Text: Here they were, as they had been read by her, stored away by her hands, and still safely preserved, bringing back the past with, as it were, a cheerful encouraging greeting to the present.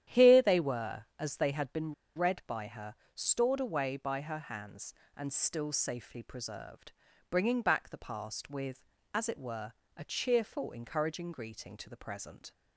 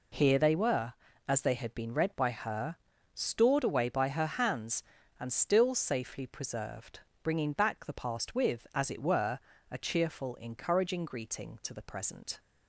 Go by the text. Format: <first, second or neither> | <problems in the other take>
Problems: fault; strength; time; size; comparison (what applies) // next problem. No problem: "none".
second | starts louder than the rest; strong; until 1.2 s; 10.5 dB // pauses between "been" and "read"; slight; at 1.9 s; 0.23 s long